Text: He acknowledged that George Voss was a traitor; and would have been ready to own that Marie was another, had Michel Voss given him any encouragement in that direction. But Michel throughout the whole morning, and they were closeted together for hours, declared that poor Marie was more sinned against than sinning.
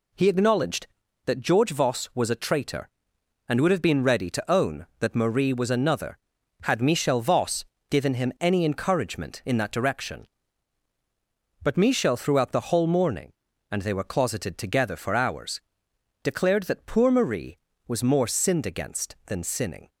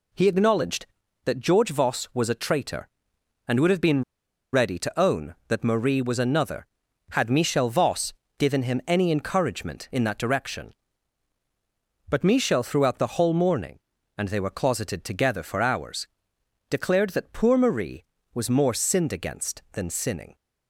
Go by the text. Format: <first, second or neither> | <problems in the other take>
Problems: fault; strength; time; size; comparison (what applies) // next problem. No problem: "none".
first | pauses between "been" and "ready"; noticeable; at 4.0 s; 0.51 s long // pauses between "Voss" and "given"; slight; at 8.1 s; 0.24 s long; slight in the first